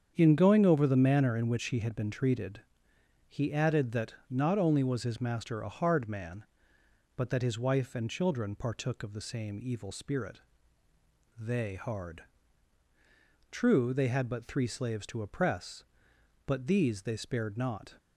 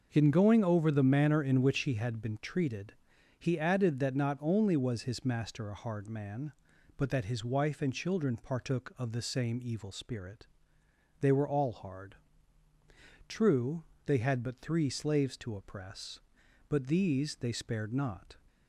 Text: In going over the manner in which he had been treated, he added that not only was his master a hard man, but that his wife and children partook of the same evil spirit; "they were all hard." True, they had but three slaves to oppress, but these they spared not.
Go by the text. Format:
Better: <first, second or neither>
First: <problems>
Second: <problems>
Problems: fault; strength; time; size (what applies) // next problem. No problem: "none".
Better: second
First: starts louder than the rest; strong; until 1.1 s; 8 dB // pauses between "that" and "not"; slight; at 4.1 s; 0.16 s long // skips "were all"; at 11.7 s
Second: starts louder than the rest; noticeable; until 1.1 s; 6 dB